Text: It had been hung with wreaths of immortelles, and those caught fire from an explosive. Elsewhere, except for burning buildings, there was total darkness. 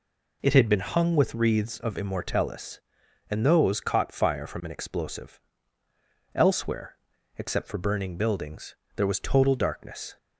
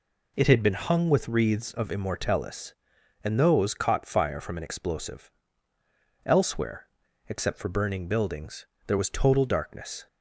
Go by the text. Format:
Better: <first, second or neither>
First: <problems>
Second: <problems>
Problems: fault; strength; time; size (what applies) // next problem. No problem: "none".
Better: neither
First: none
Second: none